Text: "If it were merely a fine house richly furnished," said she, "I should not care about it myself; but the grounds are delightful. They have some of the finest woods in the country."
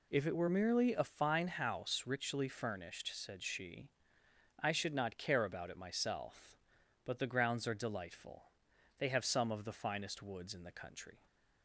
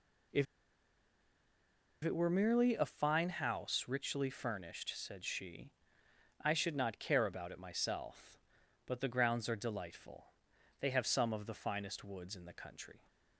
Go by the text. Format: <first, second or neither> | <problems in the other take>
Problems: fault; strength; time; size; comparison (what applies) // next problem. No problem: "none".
first | pauses between "If" and "it"; strong; at 0.4 s; 1.5 s long